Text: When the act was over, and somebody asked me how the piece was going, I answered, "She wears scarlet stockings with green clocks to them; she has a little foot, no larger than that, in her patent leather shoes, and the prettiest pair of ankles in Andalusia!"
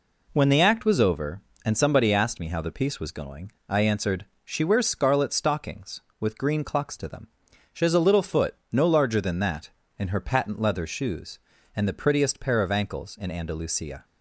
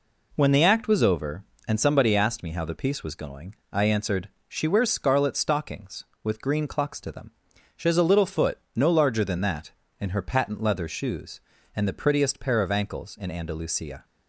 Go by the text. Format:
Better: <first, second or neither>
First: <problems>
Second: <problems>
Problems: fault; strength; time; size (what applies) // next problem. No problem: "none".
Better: neither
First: none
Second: none